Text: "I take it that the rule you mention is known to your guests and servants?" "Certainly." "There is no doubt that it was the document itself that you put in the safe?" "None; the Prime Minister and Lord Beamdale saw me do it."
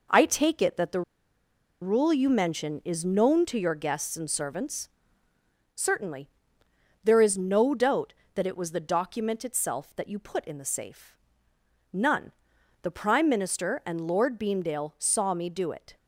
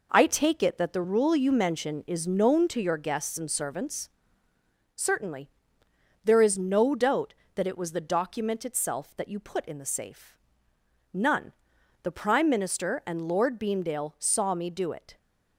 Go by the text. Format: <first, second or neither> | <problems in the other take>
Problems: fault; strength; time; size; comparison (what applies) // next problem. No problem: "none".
second | pauses between "the" and "rule"; noticeable; at 1.0 s; 0.80 s long